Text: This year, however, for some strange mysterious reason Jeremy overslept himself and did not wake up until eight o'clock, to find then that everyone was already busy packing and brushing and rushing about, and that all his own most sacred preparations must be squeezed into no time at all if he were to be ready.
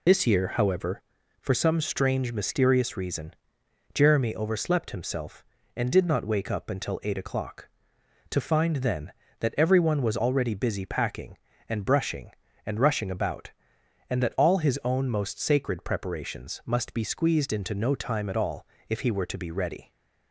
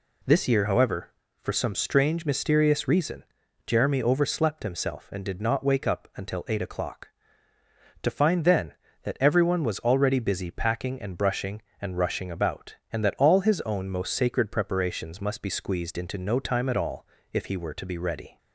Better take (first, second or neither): second